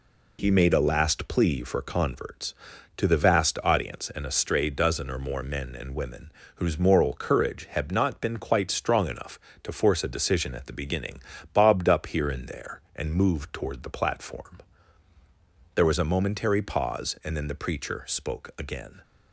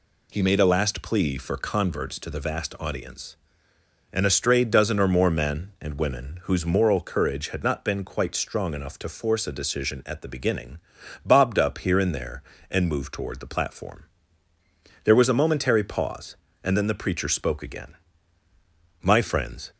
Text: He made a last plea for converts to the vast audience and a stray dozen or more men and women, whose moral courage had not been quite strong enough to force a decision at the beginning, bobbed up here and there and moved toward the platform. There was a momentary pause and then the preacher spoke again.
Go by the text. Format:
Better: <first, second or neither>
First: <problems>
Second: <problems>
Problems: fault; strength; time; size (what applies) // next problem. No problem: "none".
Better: first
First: none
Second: goes on to say "My friends"; noticeable; from 19.0 s on; 0.70 s long